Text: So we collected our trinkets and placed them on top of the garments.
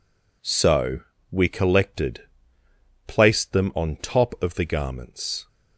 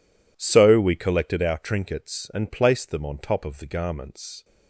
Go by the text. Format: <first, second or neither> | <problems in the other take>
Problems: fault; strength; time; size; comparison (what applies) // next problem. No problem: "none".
second | pauses between "So" and "we"; slight; at 0.9 s; 0.32 s long // skips "our trinkets and"; at 2.6 s